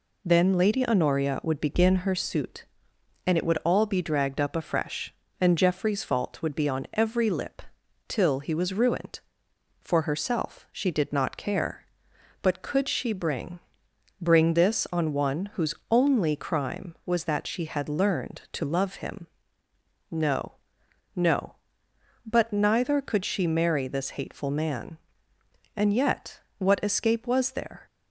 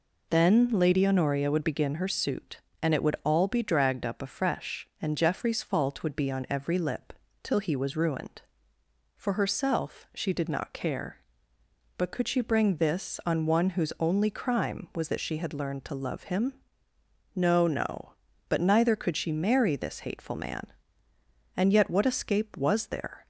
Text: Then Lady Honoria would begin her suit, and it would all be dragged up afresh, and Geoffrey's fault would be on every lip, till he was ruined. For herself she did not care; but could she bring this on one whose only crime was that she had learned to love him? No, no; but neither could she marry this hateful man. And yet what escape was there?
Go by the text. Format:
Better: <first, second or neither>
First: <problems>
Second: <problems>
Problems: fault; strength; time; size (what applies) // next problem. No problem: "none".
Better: second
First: says "bring" twice; at 14.2 s // pauses between "yet" and "what"; slight; at 26.4 s; 0.18 s long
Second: none